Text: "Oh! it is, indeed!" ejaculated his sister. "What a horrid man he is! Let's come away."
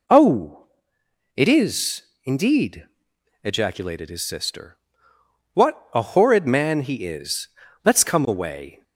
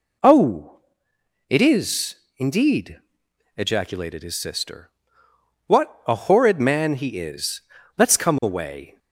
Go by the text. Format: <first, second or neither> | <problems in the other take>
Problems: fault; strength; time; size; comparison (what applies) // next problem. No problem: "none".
neither | none